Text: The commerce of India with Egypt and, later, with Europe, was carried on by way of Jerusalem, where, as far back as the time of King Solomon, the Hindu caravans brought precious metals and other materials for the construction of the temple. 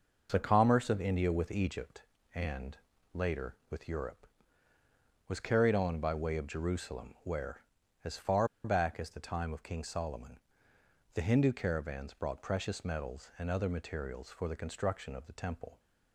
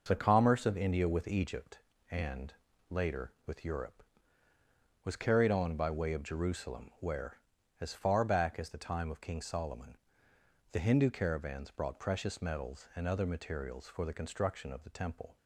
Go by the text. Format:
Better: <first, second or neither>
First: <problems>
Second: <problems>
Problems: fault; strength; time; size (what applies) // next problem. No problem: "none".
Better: second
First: pauses between "far" and "back"; slight; at 8.4 s; 0.17 s long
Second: none